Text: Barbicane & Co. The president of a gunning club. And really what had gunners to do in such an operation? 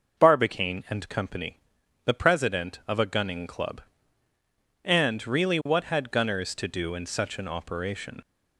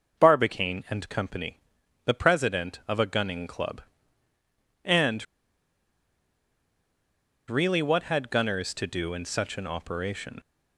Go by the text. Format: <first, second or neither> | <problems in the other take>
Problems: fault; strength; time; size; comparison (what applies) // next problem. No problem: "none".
first | pauses between "And" and "really"; strong; at 5.2 s; 2.2 s long